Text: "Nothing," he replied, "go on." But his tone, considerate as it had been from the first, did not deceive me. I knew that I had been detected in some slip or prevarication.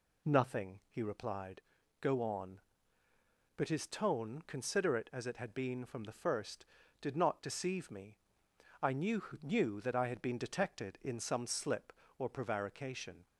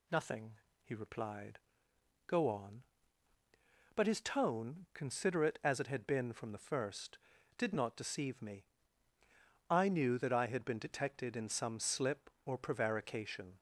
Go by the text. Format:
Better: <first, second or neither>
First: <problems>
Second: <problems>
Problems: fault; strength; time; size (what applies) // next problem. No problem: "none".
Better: second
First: says "knew" twice; at 9.4 s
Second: none